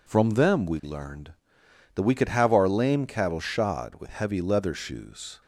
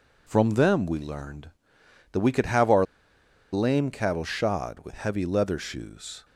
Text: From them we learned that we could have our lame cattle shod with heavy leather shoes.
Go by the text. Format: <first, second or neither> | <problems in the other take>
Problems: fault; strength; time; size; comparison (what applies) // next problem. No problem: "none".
first | pauses between "our" and "lame"; noticeable; at 2.8 s; 0.68 s long